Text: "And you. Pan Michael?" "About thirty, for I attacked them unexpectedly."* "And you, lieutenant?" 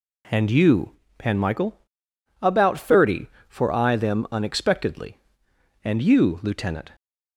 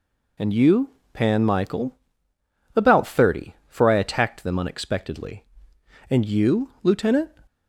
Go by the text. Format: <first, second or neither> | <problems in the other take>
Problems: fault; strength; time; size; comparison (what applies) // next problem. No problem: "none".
second | skips "attacked"; at 3.9 s